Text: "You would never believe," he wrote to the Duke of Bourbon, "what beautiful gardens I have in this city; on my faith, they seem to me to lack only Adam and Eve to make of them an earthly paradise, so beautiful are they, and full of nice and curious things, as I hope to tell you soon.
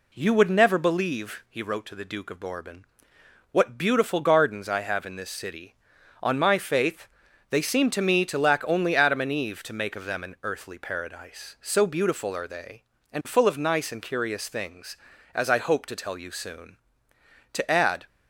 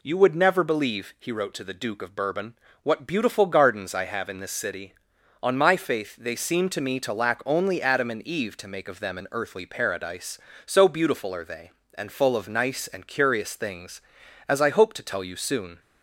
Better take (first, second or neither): second